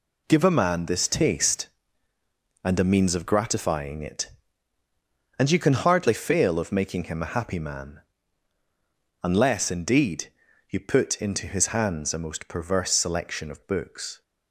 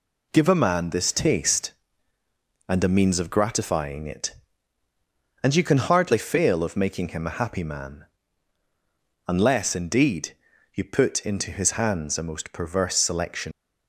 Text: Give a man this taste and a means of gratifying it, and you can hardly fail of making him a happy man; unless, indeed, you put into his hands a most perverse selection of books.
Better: first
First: none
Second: stops before "of books"; at 13.5 s

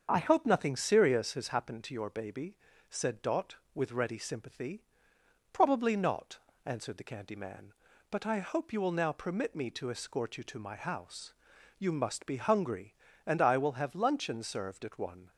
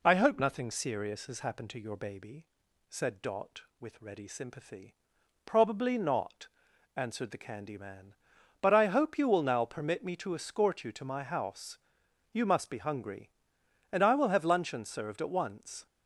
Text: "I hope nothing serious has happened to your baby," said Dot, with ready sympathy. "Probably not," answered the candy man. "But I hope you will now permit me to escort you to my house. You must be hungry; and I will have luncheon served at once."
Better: second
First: starts louder than the rest; until 1.1 s; 7 dB // says "one" for "once"; at 14.9 s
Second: none

